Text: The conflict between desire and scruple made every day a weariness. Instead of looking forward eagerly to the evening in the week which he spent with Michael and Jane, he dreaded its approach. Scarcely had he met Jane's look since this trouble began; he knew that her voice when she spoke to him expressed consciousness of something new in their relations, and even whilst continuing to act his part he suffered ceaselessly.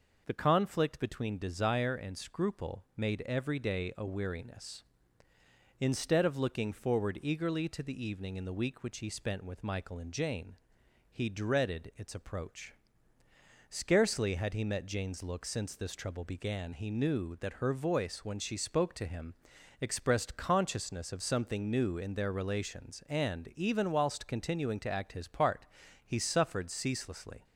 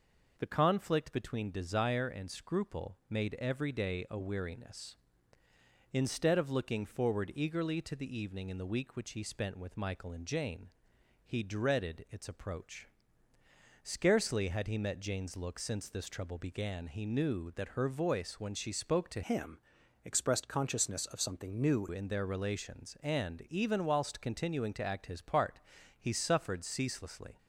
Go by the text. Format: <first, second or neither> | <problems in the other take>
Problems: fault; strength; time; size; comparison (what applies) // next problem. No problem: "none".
first | changes voice from "him" to "new"; from 19.2 to 21.8 s; 2.6 s long // pauses between "him" and "expressed"; at 19.6 s; 0.42 s long; noticeable in the first // pauses between "part" and "he"; at 25.5 s; 0.40 s long; also in the first